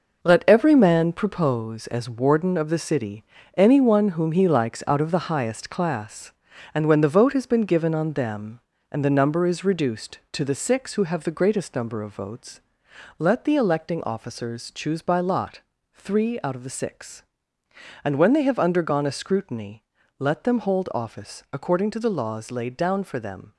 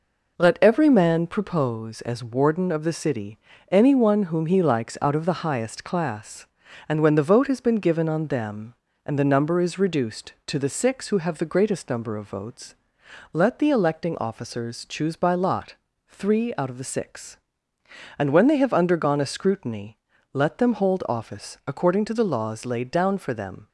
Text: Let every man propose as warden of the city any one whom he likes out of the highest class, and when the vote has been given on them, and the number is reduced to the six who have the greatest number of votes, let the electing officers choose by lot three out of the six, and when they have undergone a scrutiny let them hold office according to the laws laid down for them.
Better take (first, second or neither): second